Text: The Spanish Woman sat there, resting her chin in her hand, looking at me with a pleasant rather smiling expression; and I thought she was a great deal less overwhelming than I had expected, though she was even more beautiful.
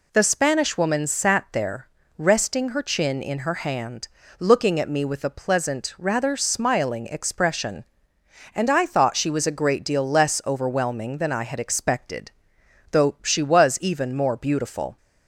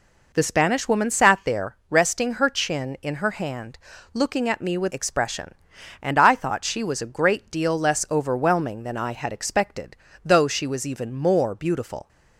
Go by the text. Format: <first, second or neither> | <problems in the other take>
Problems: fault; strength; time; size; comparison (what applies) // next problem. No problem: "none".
first | skips "a pleasant rather smiling"; at 4.9 s